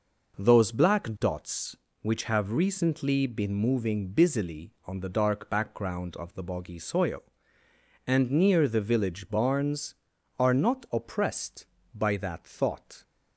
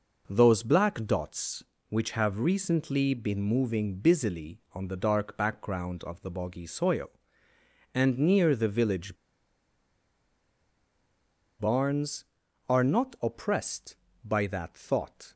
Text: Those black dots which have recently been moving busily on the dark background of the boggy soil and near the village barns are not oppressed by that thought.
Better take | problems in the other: first | pauses between "village" and "barns"; strong; at 9.1 s; 2.4 s long

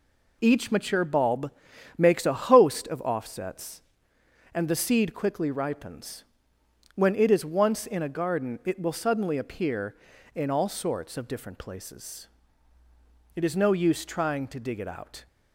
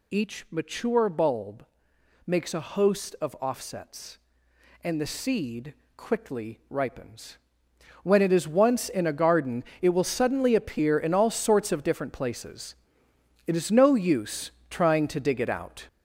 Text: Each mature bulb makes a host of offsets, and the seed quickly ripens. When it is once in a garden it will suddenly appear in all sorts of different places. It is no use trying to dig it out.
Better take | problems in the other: first | gets louder; noticeable; throughout; 5.5 dB // pauses between "bulb" and "makes"; noticeable; at 1.6 s; 0.62 s long; noticeable in the first // pauses between "seed" and "quickly"; slight; at 5.7 s; 0.24 s long // pauses between "garden" and "it"; slight; at 9.6 s; 0.18 s long // pauses between "use" and "trying"; slight; at 14.5 s; 0.18 s long

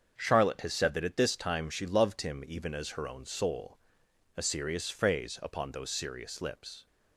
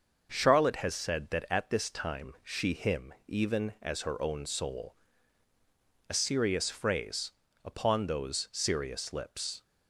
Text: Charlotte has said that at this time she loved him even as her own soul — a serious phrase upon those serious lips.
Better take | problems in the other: first | starts louder than the rest; until 1.3 s; 6 dB; also in the first // skips "loved"; at 2.7 s // pauses between "phrase" and "upon"; slight; at 7.3 s; 0.32 s long

